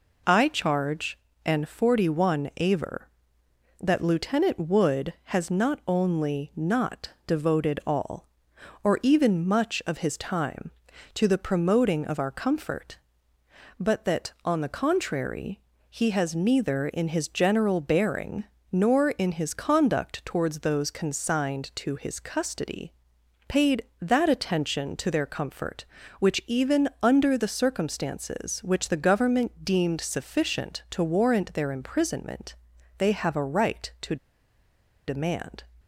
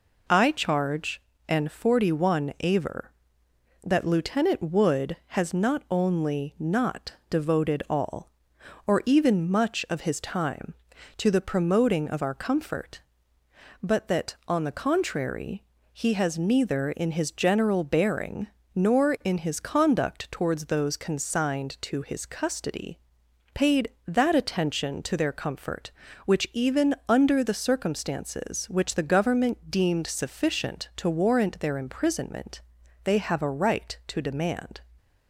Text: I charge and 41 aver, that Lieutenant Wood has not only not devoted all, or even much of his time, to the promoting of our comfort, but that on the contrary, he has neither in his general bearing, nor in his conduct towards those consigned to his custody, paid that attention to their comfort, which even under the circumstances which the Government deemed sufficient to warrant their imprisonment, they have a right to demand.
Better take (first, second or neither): second